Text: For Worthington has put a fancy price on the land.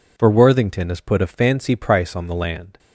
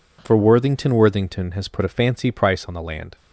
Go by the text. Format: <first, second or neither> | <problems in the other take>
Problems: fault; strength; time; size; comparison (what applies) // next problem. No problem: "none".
first | says "Worthington" twice; at 0.9 s